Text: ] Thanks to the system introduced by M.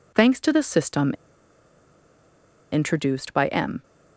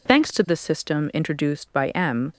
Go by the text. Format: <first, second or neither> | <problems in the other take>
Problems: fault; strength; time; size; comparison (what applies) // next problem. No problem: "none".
second | pauses between "system" and "introduced"; strong; at 1.1 s; 1.6 s long